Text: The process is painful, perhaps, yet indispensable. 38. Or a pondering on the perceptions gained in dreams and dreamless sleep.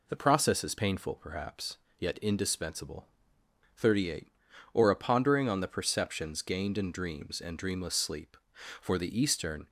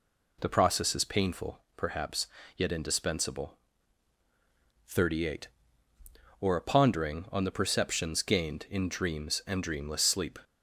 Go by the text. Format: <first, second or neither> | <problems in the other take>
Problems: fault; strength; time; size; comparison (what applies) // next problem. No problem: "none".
second | goes on to say "For the Eastern"; noticeable; from 8.8 s on; 0.88 s long